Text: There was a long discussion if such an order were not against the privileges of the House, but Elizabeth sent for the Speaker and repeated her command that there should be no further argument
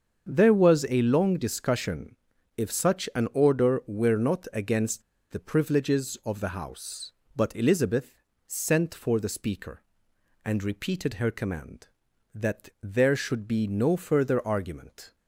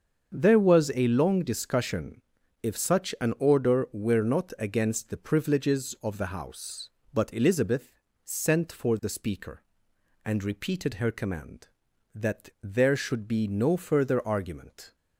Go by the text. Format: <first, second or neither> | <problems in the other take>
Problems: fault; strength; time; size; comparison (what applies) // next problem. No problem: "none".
second | starts louder than the rest; until 1.3 s; 7 dB; also in the second // pauses between "discussion" and "if"; at 2.1 s; 0.40 s long; also in the second // pauses between "against" and "the"; slight; at 5.0 s; 0.31 s long // pauses between "Elizabeth" and "sent"; slight; at 8.2 s; 0.26 s long; slight in the second